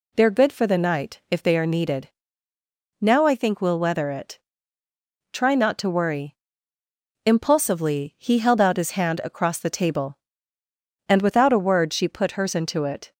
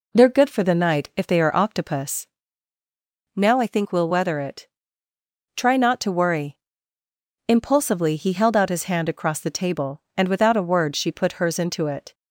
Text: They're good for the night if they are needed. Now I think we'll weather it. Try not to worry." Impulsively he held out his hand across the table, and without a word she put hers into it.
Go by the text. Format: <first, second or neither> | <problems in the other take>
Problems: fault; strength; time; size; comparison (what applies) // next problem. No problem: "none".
first | says "octopus" for "needed"; at 1.5 s